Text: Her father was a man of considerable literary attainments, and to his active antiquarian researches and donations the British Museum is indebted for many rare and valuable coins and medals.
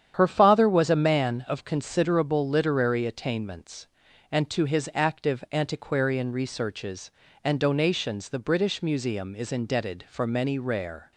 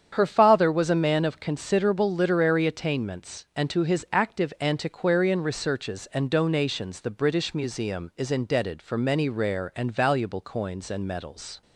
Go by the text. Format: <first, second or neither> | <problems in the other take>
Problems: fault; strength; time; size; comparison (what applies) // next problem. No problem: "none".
second | starts louder than the rest; strong; until 1.1 s; 9 dB; strong in the second // stops before "and valuable coins and medals"; at 11.1 s